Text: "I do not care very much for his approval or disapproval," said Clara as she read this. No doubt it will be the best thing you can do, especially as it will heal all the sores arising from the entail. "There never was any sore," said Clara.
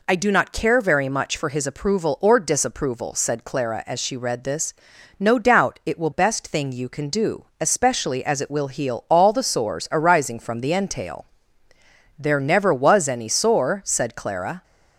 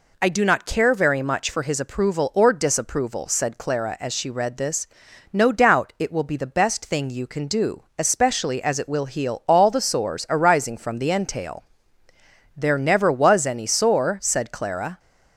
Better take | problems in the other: second | skips "be the"; at 6.1 s

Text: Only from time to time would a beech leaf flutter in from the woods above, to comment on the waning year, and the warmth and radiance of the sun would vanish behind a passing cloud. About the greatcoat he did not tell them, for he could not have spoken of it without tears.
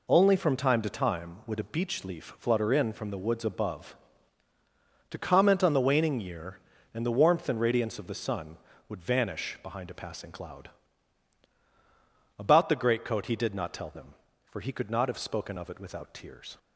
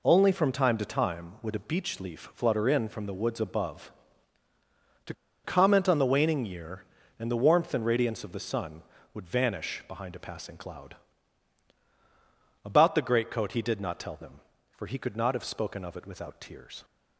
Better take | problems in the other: first | pauses between "to" and "comment"; slight; at 5.1 s; 0.31 s long

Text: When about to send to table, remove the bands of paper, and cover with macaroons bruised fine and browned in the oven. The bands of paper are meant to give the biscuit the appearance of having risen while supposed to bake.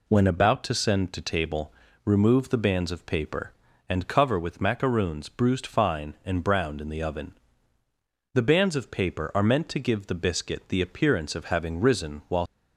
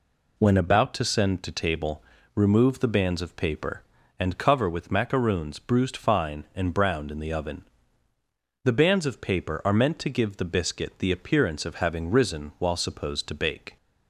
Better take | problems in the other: second | stops before "supposed to bake"; at 12.4 s

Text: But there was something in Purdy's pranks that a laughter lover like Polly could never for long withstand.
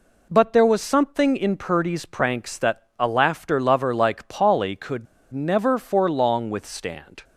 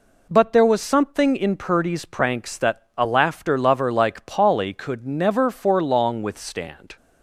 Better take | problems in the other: second | pauses between "could" and "never"; slight; at 5.0 s; 0.27 s long

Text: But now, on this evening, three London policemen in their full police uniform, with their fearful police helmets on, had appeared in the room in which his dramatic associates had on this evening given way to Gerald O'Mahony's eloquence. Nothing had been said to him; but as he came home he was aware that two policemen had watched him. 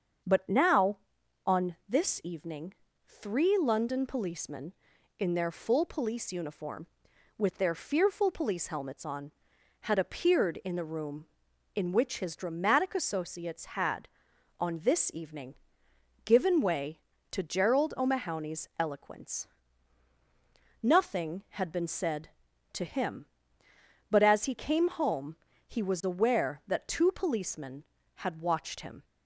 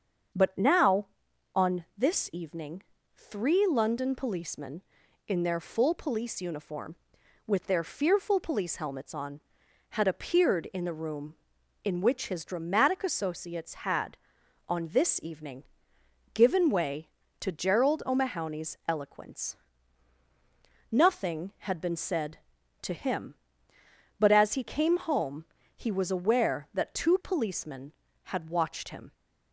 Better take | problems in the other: neither | starts louder than the rest; the same in both // pauses between "evening" and "given"; noticeable; the same in both // pauses between "home" and "he"; slight; the same in both

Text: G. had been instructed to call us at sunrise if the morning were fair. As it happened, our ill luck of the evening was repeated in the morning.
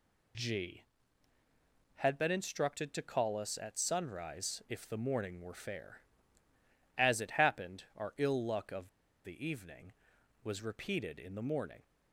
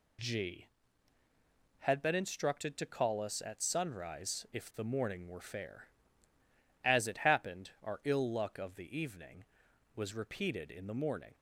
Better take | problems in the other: second | pauses between "of" and "the"; slight; at 8.8 s; 0.35 s long

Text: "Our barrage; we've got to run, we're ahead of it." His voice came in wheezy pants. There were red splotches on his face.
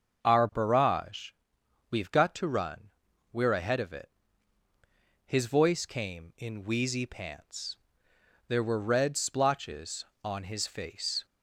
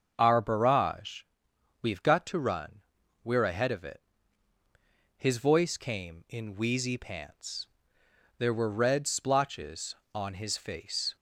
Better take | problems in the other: neither | starts louder than the rest; the same in both

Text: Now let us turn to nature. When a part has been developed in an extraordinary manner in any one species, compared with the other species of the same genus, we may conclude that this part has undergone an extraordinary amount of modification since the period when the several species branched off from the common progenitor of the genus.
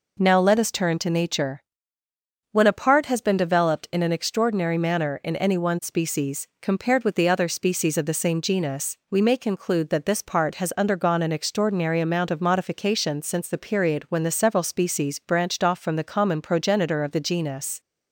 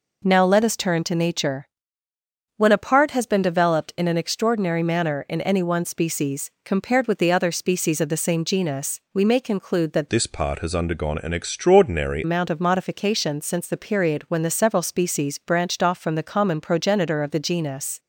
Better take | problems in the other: first | changes voice from "this" to "extraordinary"; from 10.0 to 12.2 s; 2.2 s long

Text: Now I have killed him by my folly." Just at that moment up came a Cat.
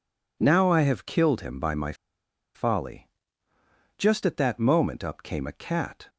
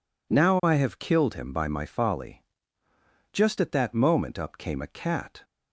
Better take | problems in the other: second | pauses between "my" and "folly"; noticeable; at 1.9 s; 0.61 s long

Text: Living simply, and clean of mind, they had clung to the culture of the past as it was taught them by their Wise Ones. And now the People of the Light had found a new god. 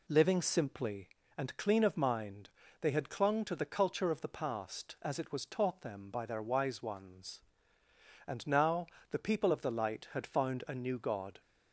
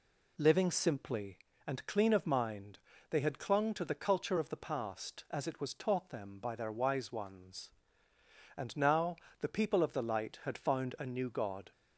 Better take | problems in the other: neither | pauses between "now" and "the"; slight; the same in both

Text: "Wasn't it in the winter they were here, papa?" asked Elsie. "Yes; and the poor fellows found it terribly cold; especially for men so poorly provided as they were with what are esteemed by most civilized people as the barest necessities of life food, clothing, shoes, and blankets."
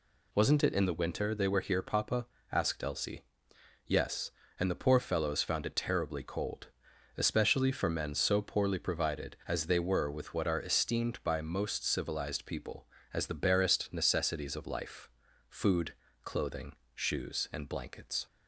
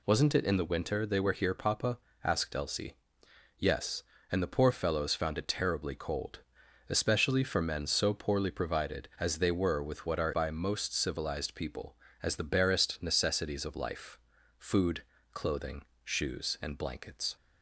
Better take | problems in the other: first | skips "esteemed"; at 10.3 s // pauses between "life" and "food"; at 14.1 s; 0.40 s long; also in the first

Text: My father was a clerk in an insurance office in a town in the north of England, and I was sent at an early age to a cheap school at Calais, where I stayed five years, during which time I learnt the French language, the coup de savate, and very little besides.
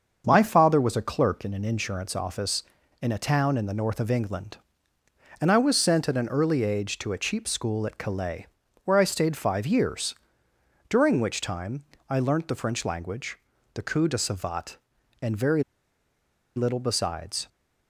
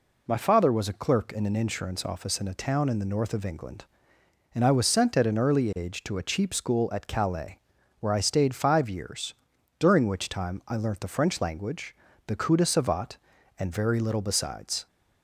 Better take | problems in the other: second | starts louder than the rest; until 1.2 s; 6.5 dB // pauses between "time" and "I"; slight; at 11.8 s; 0.26 s long // pauses between "very" and "little"; noticeable; at 15.6 s; 0.94 s long

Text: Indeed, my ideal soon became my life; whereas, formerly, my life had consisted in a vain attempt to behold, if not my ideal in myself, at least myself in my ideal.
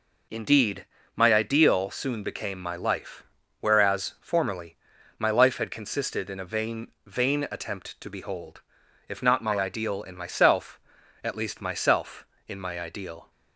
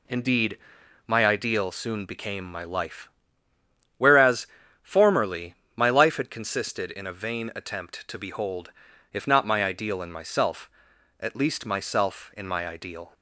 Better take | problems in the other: second | says "vain" twice; at 7.0 s

